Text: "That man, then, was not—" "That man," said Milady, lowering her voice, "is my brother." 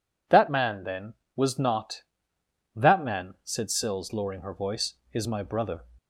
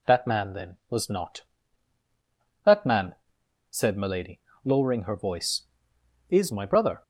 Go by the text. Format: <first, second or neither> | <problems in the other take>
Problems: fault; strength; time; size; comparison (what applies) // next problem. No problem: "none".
second | says "Sills" for "Milady"; at 3.6 s